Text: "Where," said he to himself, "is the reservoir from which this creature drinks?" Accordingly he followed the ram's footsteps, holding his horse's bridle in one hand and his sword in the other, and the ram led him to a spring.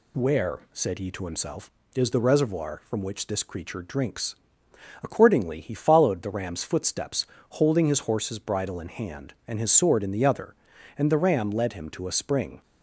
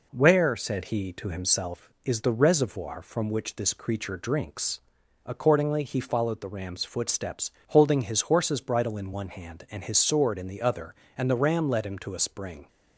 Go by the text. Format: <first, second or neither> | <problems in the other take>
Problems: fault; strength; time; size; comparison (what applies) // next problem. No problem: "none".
second | skips "one"; at 8.8 s